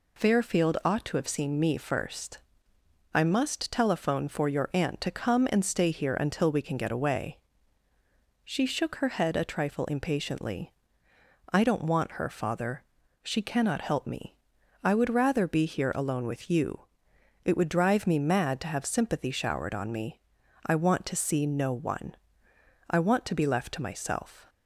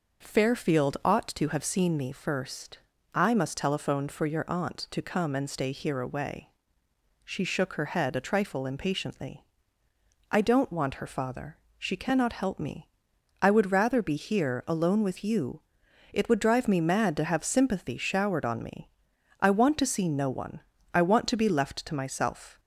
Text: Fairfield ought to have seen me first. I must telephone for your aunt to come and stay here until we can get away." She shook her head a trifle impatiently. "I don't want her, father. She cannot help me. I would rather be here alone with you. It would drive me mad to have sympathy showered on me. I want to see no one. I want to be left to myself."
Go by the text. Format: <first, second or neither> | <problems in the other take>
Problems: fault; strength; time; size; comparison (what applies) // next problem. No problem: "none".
first | skips "until we can get"; at 5.9 s